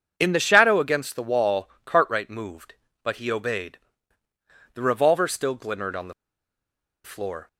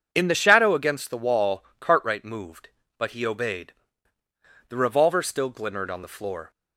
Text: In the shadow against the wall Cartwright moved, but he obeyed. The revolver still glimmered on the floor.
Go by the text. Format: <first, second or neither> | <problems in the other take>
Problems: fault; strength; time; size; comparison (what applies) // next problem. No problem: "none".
second | pauses between "wall" and "Cartwright"; slight; at 1.6 s; 0.16 s long; slight in the second // pauses between "the" and "floor"; noticeable; at 6.1 s; 0.92 s long